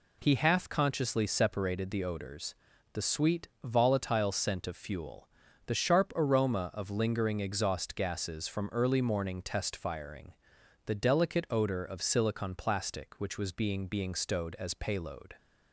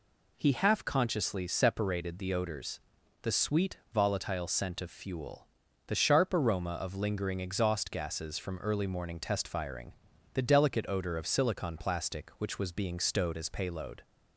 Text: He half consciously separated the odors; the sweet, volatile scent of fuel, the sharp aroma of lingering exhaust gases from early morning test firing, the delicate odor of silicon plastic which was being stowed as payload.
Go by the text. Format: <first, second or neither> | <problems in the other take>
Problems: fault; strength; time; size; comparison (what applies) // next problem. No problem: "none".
second | says "being" twice; at 13.8 s